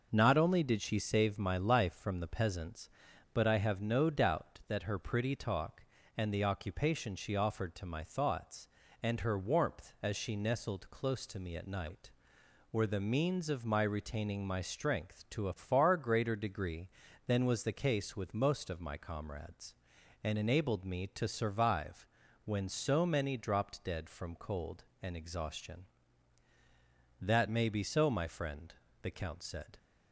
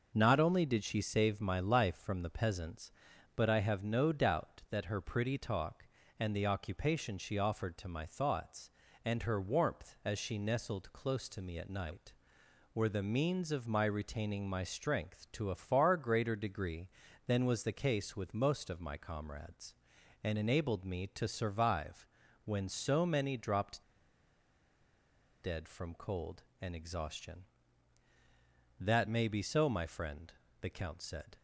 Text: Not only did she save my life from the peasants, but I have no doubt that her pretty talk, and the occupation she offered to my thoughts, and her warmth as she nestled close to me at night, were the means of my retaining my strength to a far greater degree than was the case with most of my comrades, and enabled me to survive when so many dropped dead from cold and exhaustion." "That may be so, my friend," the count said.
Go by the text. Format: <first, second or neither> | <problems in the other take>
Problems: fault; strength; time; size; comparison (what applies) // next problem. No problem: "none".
first | pauses between "survive" and "when"; at 22.0 s; 0.40 s long; also in the first // pauses between "dropped" and "dead"; strong; at 23.8 s; 1.5 s long